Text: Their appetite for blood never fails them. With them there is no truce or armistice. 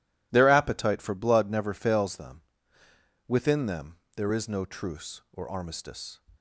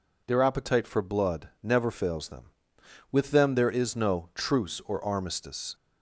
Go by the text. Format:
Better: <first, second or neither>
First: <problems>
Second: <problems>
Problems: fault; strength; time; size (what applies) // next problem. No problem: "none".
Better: second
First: says "Within" for "With"; at 3.2 s // pauses between "them" and "there"; slight; at 3.9 s; 0.18 s long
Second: none